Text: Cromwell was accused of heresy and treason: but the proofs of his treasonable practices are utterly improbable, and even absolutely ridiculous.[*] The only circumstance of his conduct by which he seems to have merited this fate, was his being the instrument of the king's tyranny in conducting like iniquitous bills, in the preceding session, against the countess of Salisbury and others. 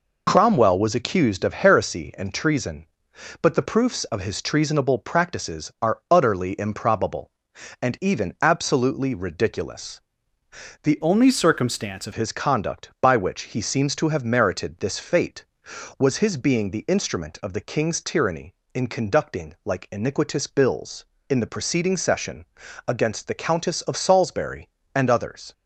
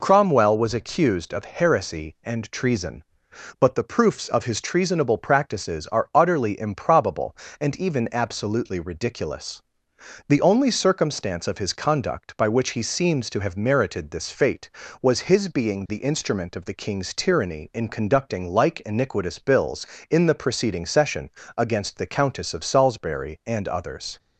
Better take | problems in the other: second | changes voice from "only" to "of"; from 11.0 to 12.1 s; 1.1 s long

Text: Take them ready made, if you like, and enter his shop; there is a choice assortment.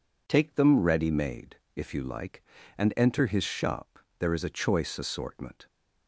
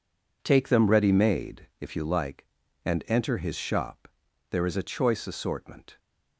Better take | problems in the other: neither | none

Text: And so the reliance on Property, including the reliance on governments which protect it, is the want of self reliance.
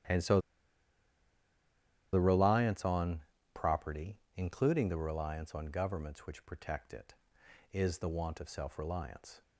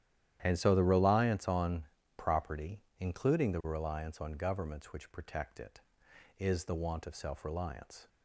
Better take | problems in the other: second | starts louder than the rest; strong; until 2.8 s; 11.5 dB; strong in the second // pauses between "so" and "the"; strong; at 0.3 s; 1.7 s long // pauses between "on" and "Property"; slight; at 3.1 s; 0.34 s long; slight in the second

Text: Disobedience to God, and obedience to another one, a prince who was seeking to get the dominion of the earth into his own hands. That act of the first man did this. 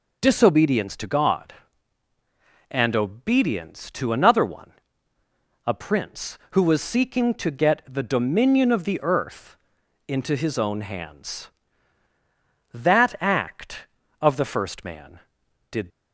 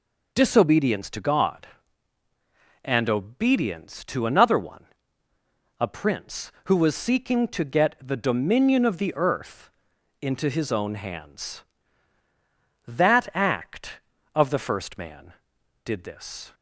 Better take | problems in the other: second | pauses between "earth" and "into"; noticeable; at 9.5 s; 0.52 s long; noticeable in the second // stops before "this"; at 15.9 s

